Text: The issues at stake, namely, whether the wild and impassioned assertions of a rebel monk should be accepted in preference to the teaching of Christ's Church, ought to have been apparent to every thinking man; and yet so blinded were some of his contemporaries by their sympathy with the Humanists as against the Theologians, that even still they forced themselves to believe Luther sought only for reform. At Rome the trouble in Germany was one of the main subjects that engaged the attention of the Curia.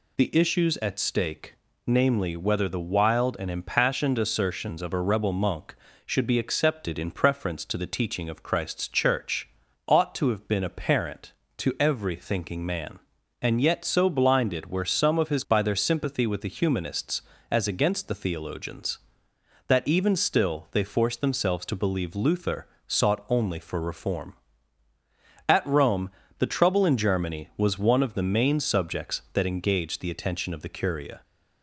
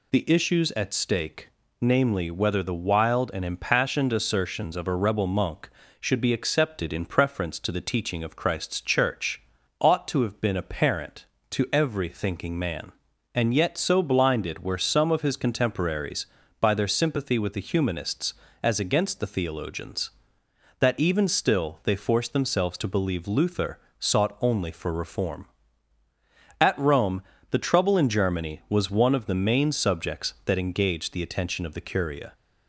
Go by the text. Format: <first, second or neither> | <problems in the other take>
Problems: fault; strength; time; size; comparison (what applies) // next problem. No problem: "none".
second | skips "contemporaries"; at 15.4 s // pauses between "Luther" and "sought"; slight; at 22.6 s; 0.20 s long; slight in the second // pauses between "Rome" and "the"; slight; at 26.1 s; 0.28 s long; slight in the second